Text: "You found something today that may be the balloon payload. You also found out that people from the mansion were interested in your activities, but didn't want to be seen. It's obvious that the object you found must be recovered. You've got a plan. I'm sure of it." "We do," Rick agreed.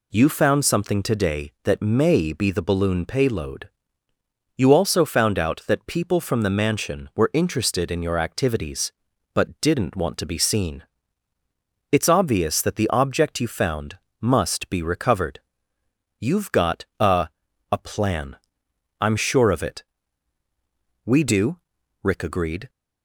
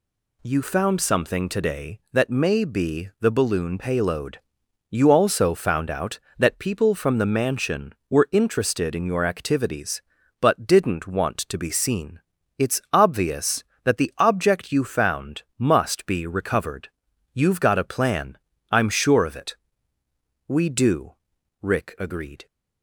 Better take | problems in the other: second | pauses between "found" and "must"; slight; at 13.9 s; 0.20 s long // says "a" twice; at 17.7 s

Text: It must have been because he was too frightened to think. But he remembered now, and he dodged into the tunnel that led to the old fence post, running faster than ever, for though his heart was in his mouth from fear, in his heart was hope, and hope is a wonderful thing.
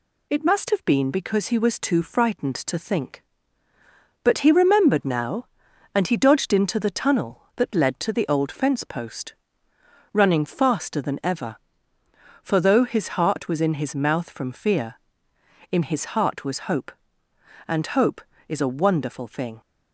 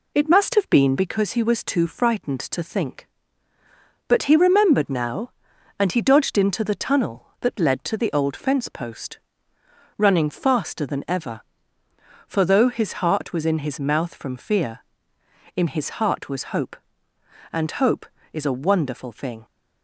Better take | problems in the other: first | starts louder than the rest; slight; until 1.2 s; 2.5 dB

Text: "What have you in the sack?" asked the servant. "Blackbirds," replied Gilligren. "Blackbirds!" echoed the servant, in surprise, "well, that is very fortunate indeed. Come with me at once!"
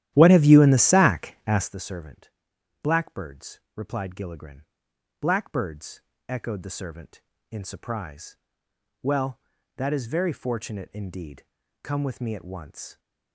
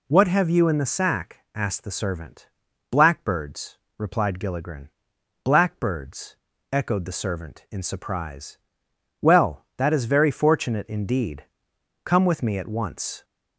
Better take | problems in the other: second | starts louder than the rest; strong; until 1.7 s; 12.5 dB

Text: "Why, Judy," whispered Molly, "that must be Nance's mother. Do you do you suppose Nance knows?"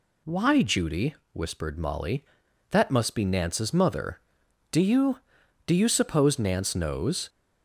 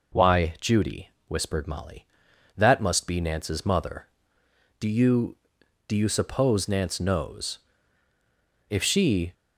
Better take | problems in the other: first | goes on to say "If she"; noticeable; from 8.6 s on; 0.64 s long

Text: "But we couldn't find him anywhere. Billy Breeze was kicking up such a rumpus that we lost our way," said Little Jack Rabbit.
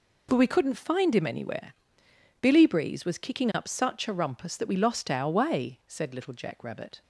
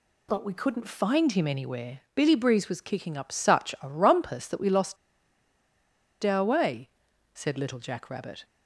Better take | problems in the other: first | pauses between "lost" and "our"; strong; at 4.9 s; 1.2 s long

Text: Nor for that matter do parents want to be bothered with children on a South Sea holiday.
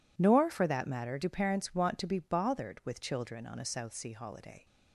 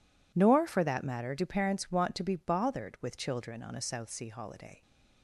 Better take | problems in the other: neither | none

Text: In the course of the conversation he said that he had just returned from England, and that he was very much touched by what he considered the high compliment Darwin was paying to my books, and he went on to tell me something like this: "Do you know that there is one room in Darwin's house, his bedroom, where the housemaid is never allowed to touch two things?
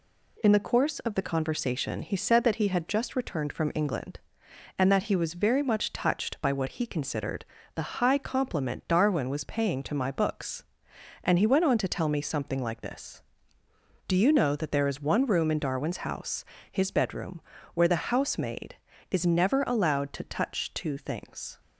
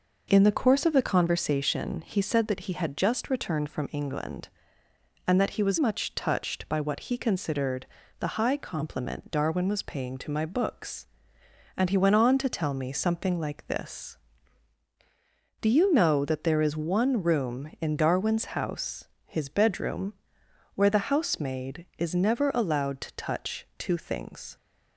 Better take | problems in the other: first | skips "very"; at 5.7 s // pauses between "considered" and "the"; slight; at 7.8 s; 0.34 s long; slight in the first

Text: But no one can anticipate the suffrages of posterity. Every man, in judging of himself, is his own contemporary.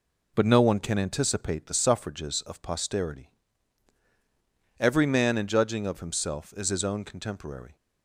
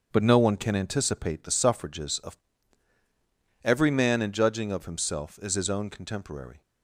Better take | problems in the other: first | skips "posterity"; at 3.0 s

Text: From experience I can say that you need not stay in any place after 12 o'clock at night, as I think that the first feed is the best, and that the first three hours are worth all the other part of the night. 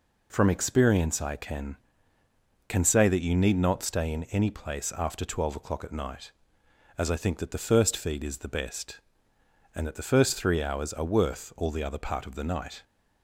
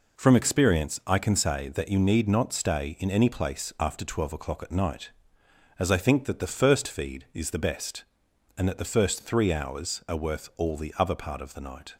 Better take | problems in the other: second | says "can" twice; at 2.6 s

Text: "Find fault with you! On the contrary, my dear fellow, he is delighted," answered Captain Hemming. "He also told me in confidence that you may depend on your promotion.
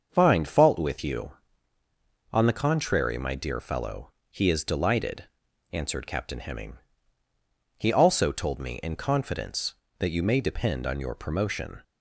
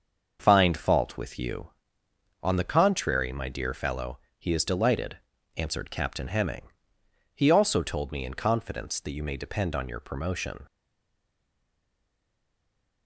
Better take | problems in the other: first | starts louder than the rest; until 1.4 s; 6.5 dB; also in the first // stays silent after the last word; from 10.6 s on; 2.4 s long

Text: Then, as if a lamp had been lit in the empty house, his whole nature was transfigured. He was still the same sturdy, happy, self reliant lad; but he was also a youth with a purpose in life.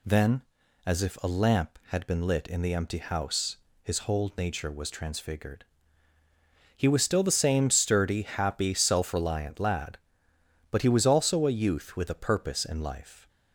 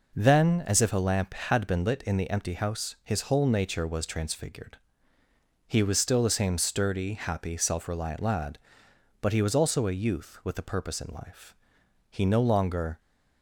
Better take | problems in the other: first | goes on to say "He no longer"; noticeable; from 12.1 s on; 0.90 s long

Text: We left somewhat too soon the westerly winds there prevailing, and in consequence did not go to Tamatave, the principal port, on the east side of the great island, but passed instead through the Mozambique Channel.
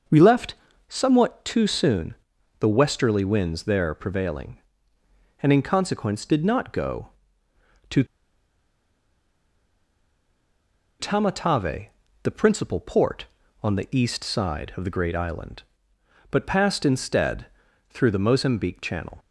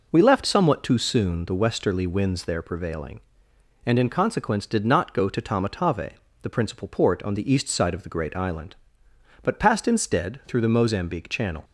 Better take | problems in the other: second | pauses between "left" and "somewhat"; slight; at 0.5 s; 0.34 s long // pauses between "soon" and "the"; at 2.1 s; 0.44 s long // pauses between "to" and "Tamatave"; strong; at 8.0 s; 2.9 s long // pauses between "instead" and "through"; at 17.4 s; 0.44 s long

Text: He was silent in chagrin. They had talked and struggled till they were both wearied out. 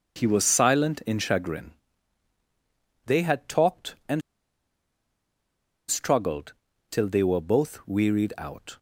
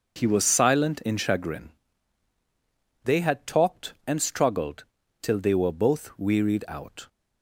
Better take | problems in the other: second | pauses between "and" and "struggled"; strong; at 4.2 s; 1.6 s long // pauses between "struggled" and "till"; slight; at 6.5 s; 0.36 s long; slight in the second

